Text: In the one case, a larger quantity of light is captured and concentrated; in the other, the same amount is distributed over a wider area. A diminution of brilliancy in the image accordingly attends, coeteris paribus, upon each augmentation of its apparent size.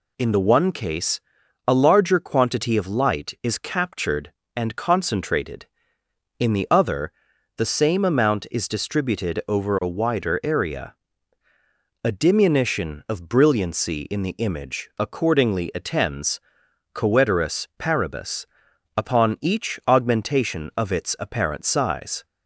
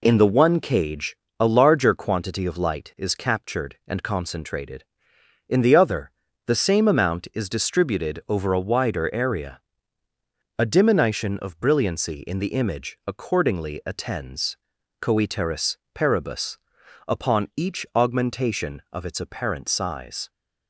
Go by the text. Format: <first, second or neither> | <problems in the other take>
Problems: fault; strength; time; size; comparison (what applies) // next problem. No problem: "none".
first | says "cage" for "case"; at 0.5 s // pauses between "coeteris" and "paribus"; slight; at 15.7 s; 0.18 s long